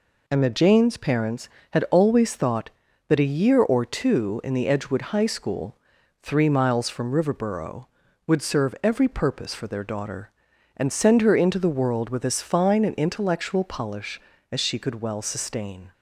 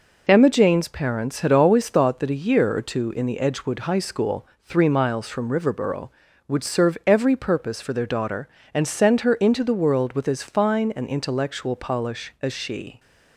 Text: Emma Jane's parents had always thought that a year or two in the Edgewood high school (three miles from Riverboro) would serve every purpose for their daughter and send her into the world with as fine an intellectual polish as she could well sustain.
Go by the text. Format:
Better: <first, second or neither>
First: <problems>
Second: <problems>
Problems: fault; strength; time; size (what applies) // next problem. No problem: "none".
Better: first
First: none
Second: stops before "could well sustain"; at 12.9 s